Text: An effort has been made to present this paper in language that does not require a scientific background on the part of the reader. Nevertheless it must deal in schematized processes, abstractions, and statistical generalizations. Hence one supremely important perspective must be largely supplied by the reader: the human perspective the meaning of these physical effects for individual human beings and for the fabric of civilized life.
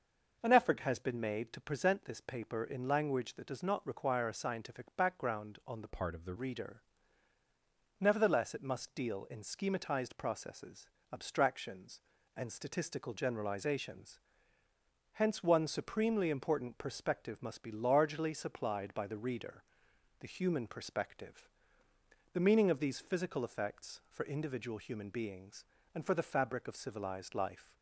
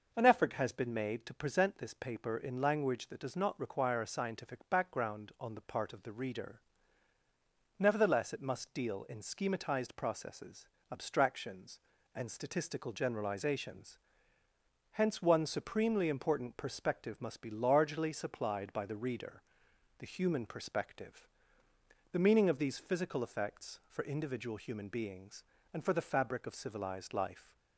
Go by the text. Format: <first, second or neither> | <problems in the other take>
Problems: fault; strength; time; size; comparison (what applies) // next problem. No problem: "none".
second | changes voice from "part" to "the"; from 5.8 to 6.3 s; 0.5 s long // pauses between "perspective" and "the"; noticeable; at 21.4 s; 0.86 s long; noticeable in the second